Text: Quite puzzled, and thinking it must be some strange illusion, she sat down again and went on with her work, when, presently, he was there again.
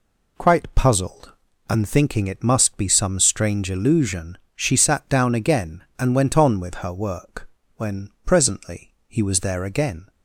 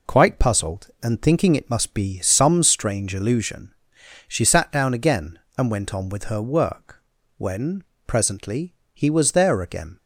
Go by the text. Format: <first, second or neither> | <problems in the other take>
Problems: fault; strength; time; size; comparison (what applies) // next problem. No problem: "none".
neither | none